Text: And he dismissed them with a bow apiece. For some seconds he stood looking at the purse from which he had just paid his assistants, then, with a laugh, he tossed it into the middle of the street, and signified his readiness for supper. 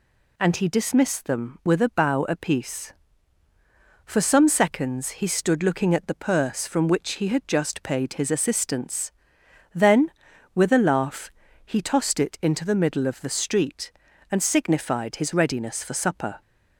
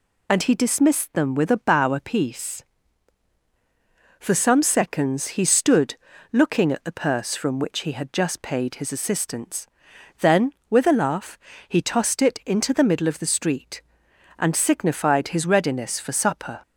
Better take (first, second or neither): first